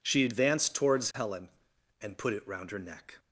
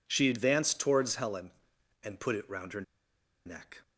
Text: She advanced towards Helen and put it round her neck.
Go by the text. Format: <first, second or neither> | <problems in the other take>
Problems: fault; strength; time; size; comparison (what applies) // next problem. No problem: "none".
first | pauses between "her" and "neck"; noticeable; at 2.8 s; 0.63 s long